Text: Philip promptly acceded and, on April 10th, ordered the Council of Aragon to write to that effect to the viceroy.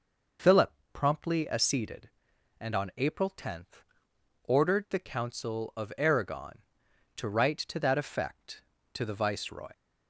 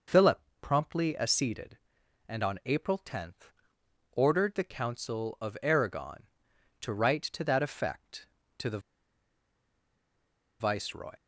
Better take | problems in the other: first | pauses between "Philip" and "promptly"; slight; at 0.4 s; 0.22 s long; slight in the first // pauses between "the" and "viceroy"; strong; at 8.7 s; 1.8 s long

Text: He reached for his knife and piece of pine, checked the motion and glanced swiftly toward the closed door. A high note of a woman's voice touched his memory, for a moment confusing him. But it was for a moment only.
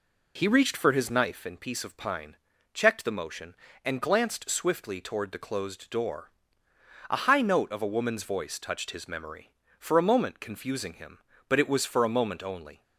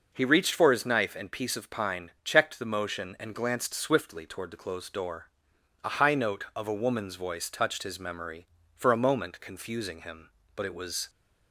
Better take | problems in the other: first | stops before "for a moment only"; at 11.0 s

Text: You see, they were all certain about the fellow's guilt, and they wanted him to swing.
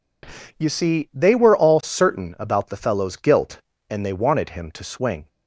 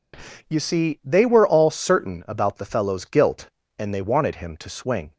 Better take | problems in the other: neither | none

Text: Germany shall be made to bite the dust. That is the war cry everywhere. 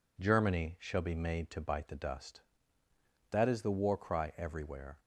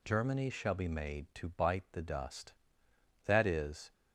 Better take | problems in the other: first | stops before "the war cry everywhere"; at 3.9 s

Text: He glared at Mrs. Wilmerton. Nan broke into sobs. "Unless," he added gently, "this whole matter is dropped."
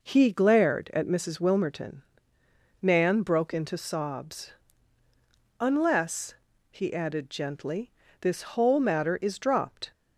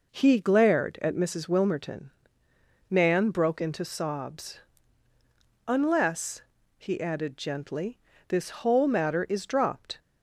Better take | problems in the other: neither | none

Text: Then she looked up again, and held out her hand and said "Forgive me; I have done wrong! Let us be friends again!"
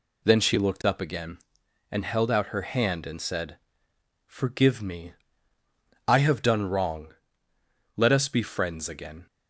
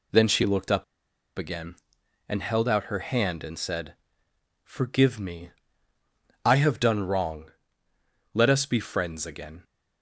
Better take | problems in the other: first | pauses between "up" and "again"; noticeable; at 0.8 s; 0.53 s long // pauses between "said" and "Forgive"; noticeable; at 3.9 s; 0.68 s long; noticeable in the first

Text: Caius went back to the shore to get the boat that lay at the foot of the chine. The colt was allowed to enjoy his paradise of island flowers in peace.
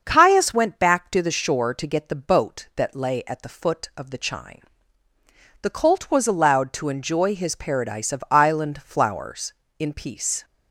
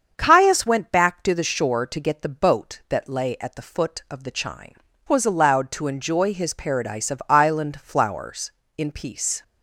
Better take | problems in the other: first | starts louder than the rest; until 1.1 s; 7 dB; also in the first // skips "The colt"; at 4.9 s

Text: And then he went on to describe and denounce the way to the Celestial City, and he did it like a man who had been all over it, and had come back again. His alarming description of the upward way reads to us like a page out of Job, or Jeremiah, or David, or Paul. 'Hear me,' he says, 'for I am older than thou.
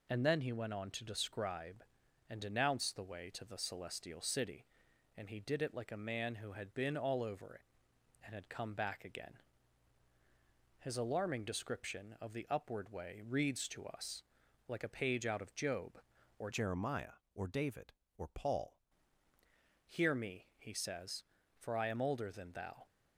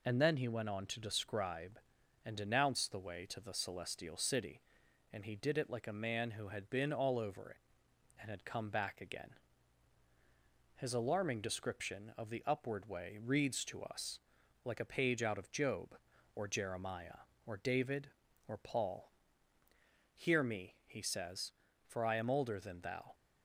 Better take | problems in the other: second | pauses between "us" and "like"; at 14.2 s; 0.44 s long; also in the second // changes voice from "Jeremiah" to "Paul"; from 16.5 to 18.8 s; 2.3 s long

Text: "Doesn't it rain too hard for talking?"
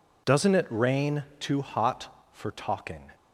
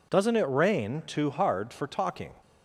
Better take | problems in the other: second | says "hot" for "hard"; at 1.5 s

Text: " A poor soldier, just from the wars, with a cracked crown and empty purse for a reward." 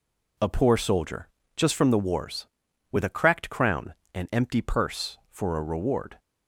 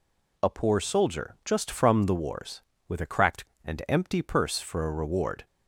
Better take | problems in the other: first | skips "crown"; at 3.5 s

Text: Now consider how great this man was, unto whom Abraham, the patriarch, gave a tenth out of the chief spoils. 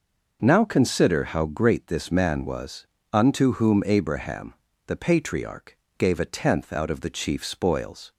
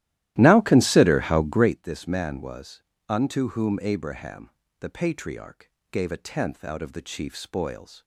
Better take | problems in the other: first | starts louder than the rest; strong; until 1.8 s; 14.5 dB

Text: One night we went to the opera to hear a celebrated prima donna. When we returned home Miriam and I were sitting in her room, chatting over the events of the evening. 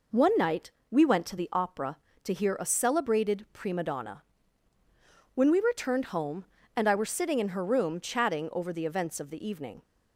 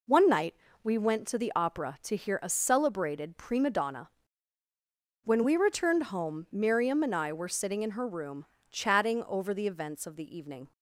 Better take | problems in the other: second | pauses between "night" and "we"; slight; at 0.7 s; 0.18 s long; slight in the second // skips "Miriam"; at 6.5 s

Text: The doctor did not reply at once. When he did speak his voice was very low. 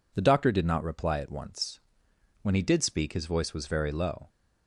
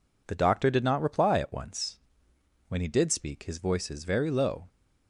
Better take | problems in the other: first | says "is" for "was"; at 3.9 s

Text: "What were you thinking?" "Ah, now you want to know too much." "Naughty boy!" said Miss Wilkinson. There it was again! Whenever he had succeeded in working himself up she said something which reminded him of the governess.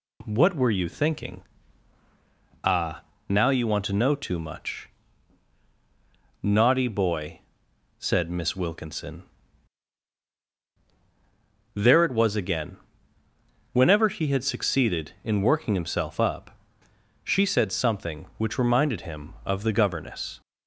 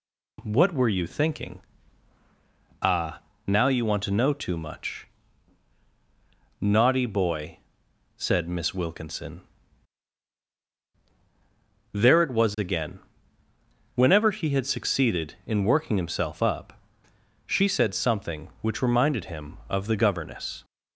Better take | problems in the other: neither | pauses between "up" and "she"; noticeable; the same in both

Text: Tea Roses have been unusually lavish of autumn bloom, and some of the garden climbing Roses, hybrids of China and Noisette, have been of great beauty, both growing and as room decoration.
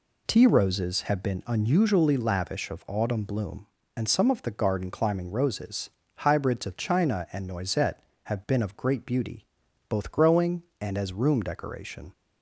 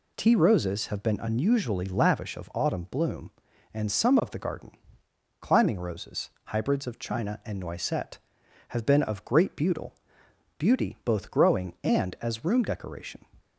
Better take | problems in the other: first | pauses between "garden" and "climbing"; noticeable; at 4.7 s; 0.70 s long // says "beauty" twice; at 10.5 s

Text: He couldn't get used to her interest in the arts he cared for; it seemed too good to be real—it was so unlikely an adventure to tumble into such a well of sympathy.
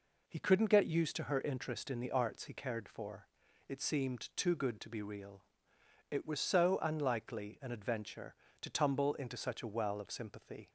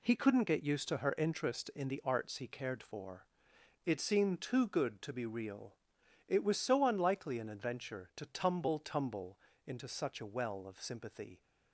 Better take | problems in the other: first | says "tumble" twice; at 8.7 s

